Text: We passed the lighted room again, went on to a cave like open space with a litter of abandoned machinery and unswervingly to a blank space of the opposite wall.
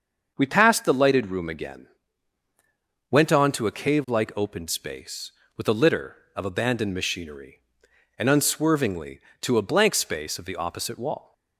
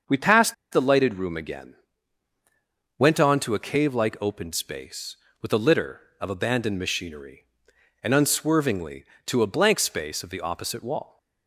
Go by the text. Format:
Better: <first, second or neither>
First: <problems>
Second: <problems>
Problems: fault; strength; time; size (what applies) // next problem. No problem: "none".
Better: first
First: starts louder than the rest; until 1.3 s; 6.5 dB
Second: starts louder than the rest; until 1.2 s; 6.5 dB // pauses between "passed" and "the"; slight; at 0.5 s; 0.16 s long